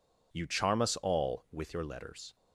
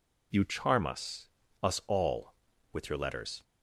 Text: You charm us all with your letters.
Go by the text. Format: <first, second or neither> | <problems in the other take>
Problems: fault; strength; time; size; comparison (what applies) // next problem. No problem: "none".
first | says "us" twice; at 1.6 s